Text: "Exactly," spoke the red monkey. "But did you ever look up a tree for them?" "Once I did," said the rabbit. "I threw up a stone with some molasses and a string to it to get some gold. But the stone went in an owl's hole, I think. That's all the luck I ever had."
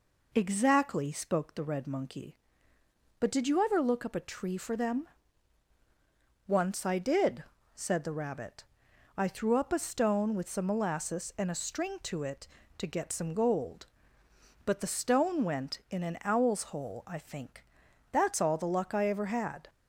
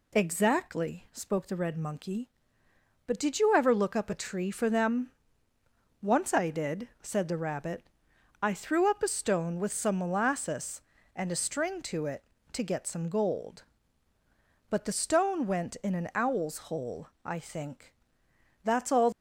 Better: first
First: none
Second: stops before "the luck I ever had"; at 19.1 s

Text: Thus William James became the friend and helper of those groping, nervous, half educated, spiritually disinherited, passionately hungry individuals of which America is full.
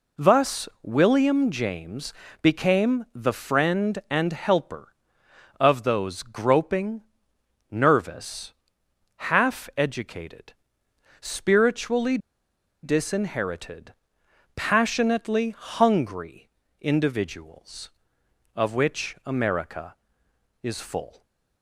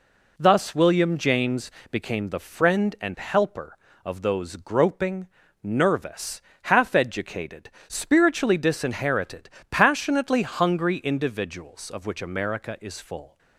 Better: second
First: pauses between "James" and "became"; slight; at 2.1 s; 0.30 s long // pauses between "spiritually" and "disinherited"; noticeable; at 12.1 s; 0.65 s long // pauses between "hungry" and "individuals"; slight; at 16.4 s; 0.32 s long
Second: pauses between "James" and "became"; slight; at 1.6 s; 0.20 s long

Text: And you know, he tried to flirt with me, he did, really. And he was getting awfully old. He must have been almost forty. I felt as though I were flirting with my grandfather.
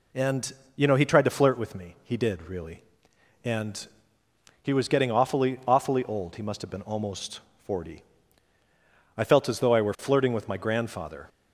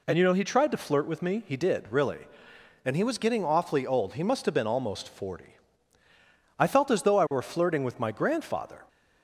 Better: second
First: pauses between "And" and "you"; slight; at 0.5 s; 0.24 s long // pauses between "And" and "he"; noticeable; at 3.8 s; 0.74 s long // says "awfully" twice; at 5.6 s // pauses between "almost" and "forty"; slight; at 7.4 s; 0.24 s long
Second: none

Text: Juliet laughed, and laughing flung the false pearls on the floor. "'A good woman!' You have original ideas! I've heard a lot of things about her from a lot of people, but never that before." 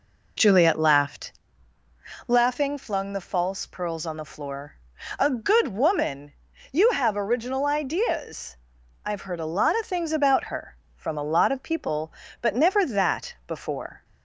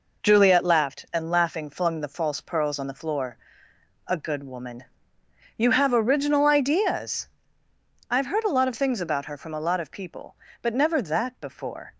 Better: second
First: skips "and"; at 1.8 s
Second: none

